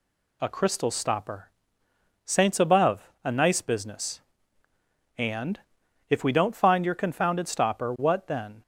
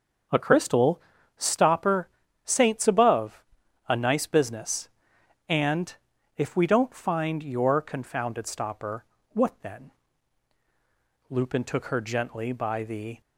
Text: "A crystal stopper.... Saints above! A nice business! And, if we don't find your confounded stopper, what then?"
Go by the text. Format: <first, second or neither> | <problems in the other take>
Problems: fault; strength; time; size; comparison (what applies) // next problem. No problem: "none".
first | starts louder than the rest; until 1.6 s; 6 dB // pauses between "crystal" and "stopper"; slight; at 1.0 s; 0.36 s long // goes on to say "Lupin took her gently by the"; strong; from 11.2 s on; 1.9 s long